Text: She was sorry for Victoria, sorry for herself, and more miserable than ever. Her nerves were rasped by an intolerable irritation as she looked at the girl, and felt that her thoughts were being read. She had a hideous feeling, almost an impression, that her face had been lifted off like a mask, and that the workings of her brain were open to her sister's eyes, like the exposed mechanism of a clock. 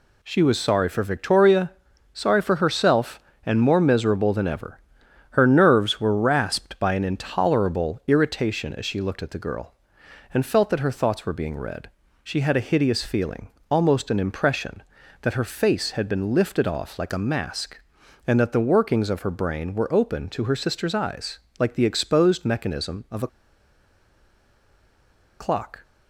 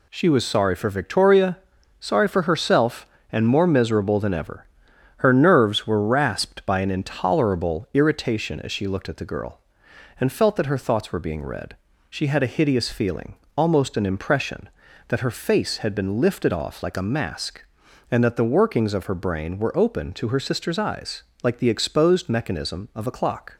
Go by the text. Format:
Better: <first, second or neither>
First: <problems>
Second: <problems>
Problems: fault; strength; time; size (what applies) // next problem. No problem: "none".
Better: second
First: pauses between "a" and "clock"; strong; at 23.2 s; 2.1 s long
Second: none